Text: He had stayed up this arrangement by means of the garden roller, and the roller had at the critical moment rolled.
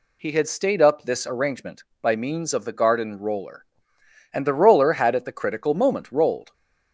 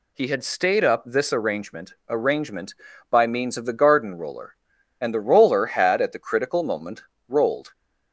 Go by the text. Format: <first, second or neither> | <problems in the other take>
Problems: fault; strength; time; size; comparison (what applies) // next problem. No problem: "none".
first | says "arrangement" twice; at 2.0 s // pauses between "moment" and "rolled"; slight; at 7.0 s; 0.26 s long